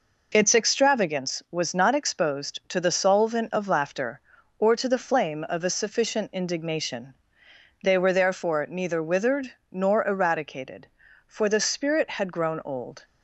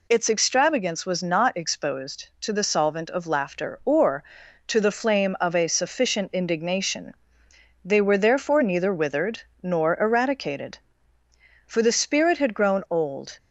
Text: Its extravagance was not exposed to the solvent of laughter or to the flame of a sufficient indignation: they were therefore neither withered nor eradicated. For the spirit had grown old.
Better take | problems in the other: neither | pauses between "withered" and "nor"; slight; the same in both

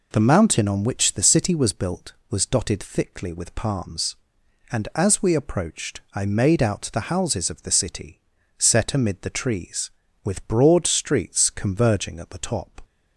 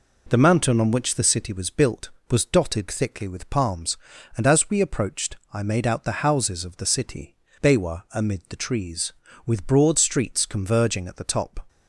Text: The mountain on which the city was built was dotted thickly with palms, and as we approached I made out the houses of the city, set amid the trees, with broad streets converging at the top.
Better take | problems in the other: first | pauses between "approached" and "I"; slight; at 5.3 s; 0.16 s long // says "bewa" for "set"; at 7.6 s

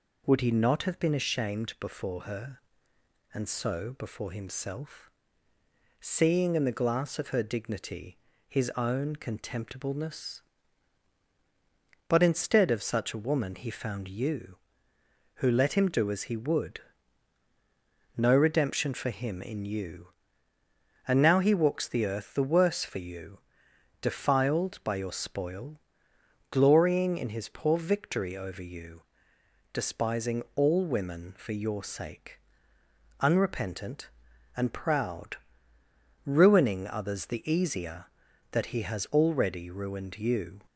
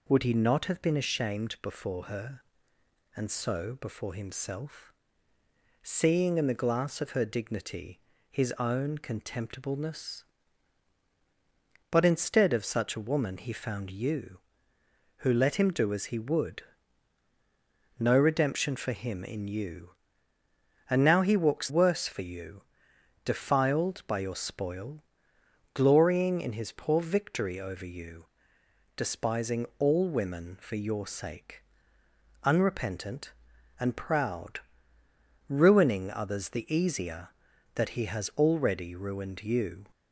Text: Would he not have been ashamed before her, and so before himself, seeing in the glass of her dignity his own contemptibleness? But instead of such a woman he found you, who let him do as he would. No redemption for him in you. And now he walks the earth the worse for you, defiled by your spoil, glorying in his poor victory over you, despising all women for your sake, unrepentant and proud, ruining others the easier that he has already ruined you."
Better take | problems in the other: first | pauses between "dignity" and "his"; slight; at 7.9 s; 0.32 s long; slight in the first // skips "the earth the"; at 21.6 s

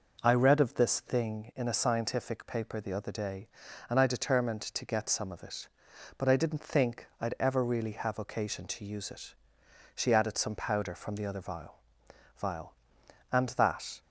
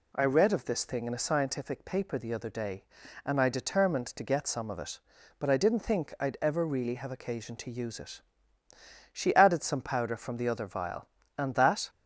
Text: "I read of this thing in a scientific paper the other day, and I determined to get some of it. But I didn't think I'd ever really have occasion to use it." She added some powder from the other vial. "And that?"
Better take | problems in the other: second | says "vial" twice; at 12.3 s

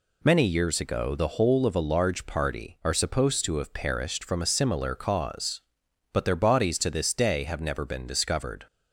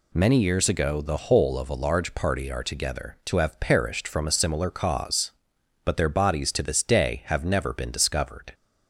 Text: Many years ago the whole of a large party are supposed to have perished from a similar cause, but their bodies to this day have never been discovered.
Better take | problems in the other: first | says "together" for "supposed"; at 2.6 s

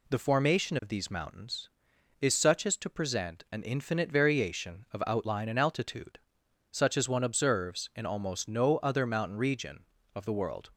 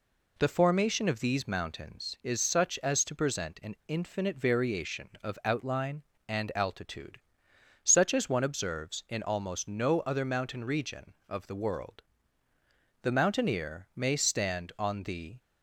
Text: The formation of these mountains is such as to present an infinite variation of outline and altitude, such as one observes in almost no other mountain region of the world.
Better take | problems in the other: first | goes on to say "The mountaineer may stand on the"; strong; from 13.0 s on; 2.3 s long

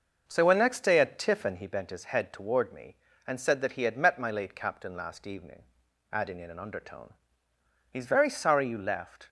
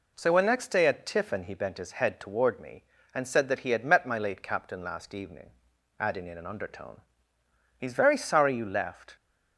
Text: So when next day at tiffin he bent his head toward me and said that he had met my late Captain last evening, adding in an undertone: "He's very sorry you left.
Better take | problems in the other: second | starts louder than the rest; noticeable; until 1.6 s; 6 dB

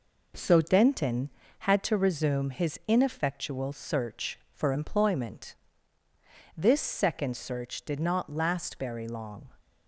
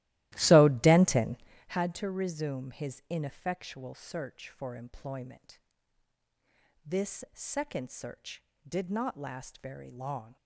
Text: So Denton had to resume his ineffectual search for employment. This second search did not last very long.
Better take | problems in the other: first | starts louder than the rest; strong; until 1.8 s; 16 dB

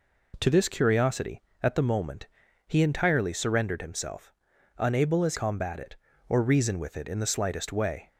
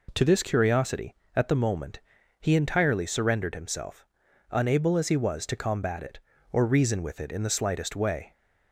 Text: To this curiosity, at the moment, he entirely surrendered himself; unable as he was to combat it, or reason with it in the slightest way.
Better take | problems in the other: second | skips "he was to"; at 5.3 s

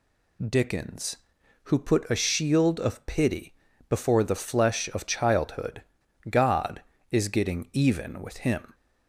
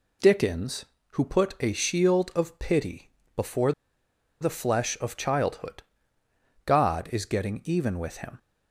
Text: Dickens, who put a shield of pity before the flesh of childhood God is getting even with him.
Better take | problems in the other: first | pauses between "pity" and "before"; slight; at 3.0 s; 0.28 s long; also in the first // pauses between "before" and "the"; noticeable; at 3.7 s; 0.69 s long // pauses between "childhood" and "God"; noticeable; at 5.8 s; 0.82 s long; noticeable in the first

